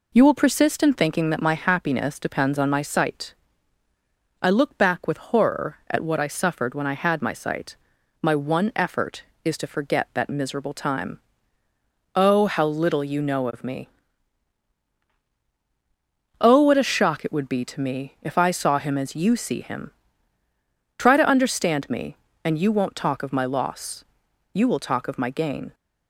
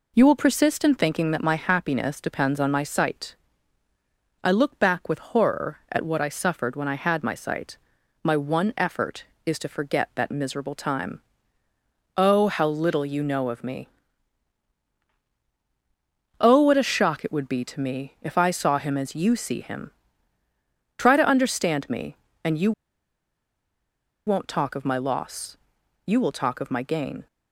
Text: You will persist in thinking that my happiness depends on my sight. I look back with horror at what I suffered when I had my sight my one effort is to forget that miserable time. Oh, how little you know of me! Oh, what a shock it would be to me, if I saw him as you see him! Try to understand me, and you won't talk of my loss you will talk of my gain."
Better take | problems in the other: first | pauses between "sight" and "my"; noticeable; at 7.7 s; 0.48 s long; noticeable in the first // pauses between "you" and "won't"; strong; at 22.7 s; 1.5 s long // pauses between "loss" and "you"; noticeable; at 25.5 s; 0.52 s long; noticeable in the first

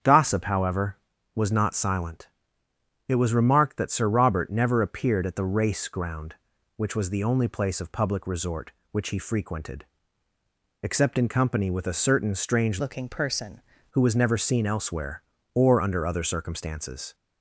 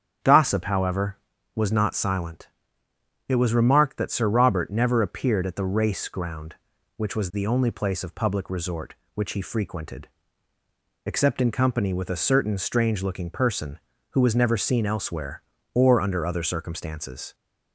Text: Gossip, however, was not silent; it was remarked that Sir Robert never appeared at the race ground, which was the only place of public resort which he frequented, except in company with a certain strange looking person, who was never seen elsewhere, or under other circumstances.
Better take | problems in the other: second | starts louder than the rest; strong; until 1.4 s; 8 dB; strong in the second // changes voice from "looking" to "person"; from 12.8 to 13.6 s; 0.8 s long

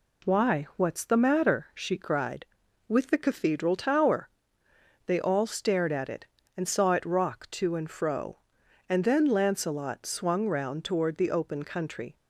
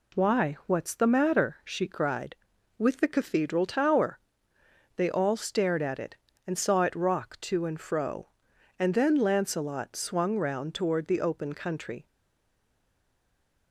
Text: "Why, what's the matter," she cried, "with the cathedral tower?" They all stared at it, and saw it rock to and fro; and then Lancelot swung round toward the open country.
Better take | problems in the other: first | stays silent after the last word; noticeable; from 12.0 s on; 1.7 s long

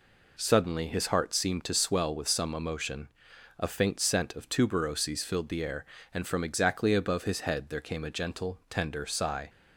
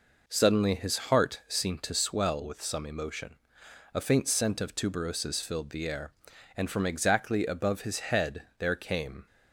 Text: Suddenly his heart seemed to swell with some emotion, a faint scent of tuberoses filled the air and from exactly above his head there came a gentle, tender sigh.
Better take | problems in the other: first | stops before "a gentle tender sigh"; at 9.2 s

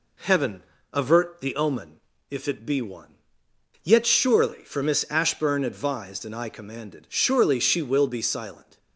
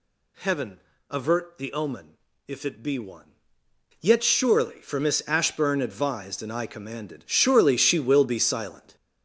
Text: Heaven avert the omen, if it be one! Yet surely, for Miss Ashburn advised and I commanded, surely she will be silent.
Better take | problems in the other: first | gets louder; strong; throughout; 9 dB // pauses between "Heaven" and "avert"; slight; at 0.8 s; 0.28 s long; slight in the first

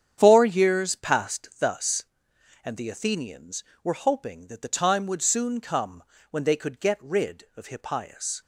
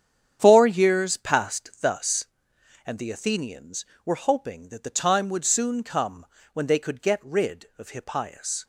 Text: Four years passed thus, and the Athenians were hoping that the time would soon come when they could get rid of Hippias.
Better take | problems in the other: neither | starts louder than the rest; strong; the same in both // pauses between "come" and "when"; slight; the same in both

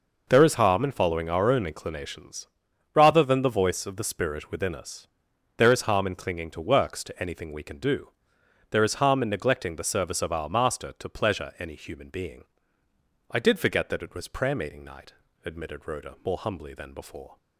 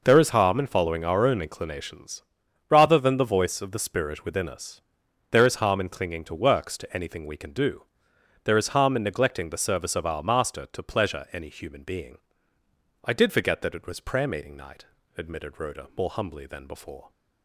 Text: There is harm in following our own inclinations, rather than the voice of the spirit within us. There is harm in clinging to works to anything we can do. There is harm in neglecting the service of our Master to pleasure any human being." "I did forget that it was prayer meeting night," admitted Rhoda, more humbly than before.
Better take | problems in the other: neither | none

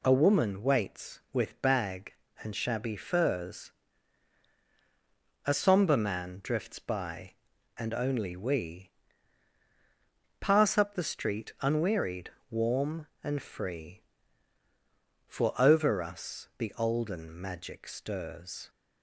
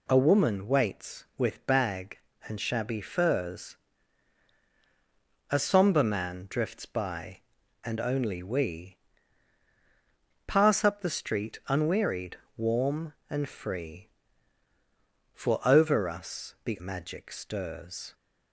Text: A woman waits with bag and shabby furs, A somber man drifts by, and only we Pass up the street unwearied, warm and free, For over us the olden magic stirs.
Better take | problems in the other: first | pauses between "we" and "Pass"; strong; at 8.9 s; 1.4 s long; strong in the first // skips "olden"; at 16.7 s

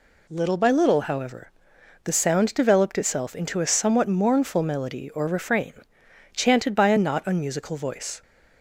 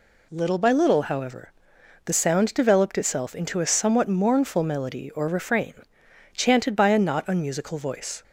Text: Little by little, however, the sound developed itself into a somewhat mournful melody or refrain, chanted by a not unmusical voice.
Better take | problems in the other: neither | none

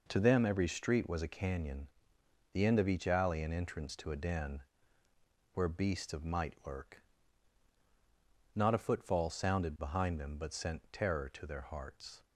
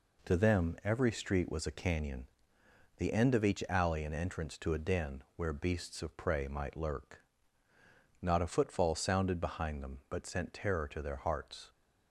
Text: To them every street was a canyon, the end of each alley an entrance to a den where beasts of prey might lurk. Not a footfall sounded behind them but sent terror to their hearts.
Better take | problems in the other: second | pauses between "den" and "where"; noticeable; at 4.6 s; 0.92 s long // skips "prey"; at 6.2 s

